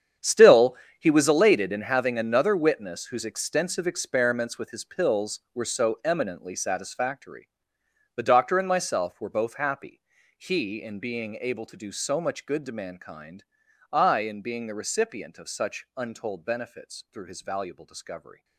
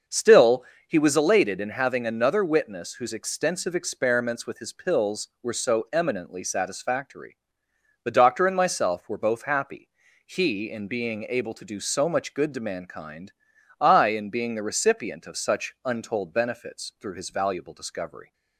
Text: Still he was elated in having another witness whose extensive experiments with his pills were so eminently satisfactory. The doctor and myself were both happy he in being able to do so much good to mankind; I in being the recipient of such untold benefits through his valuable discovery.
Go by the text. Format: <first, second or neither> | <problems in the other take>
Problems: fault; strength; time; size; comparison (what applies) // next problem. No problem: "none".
second | gets quieter; strong; throughout; 15 dB // starts louder than the rest; strong; until 1.4 s; 8.5 dB; also in the second // pauses between "Still" and "he"; slight; at 0.7 s; 0.24 s long; slight in the second // pauses between "happy" and "he"; at 10.0 s; 0.40 s long; also in the second